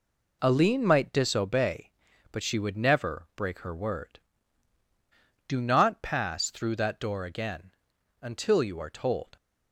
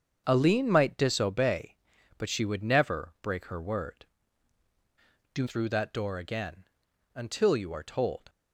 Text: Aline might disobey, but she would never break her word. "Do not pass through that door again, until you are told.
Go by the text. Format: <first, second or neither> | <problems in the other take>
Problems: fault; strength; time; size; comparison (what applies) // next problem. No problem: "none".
first | starts louder than the rest; until 1.2 s; 7 dB // skips "not pass"; at 5.4 s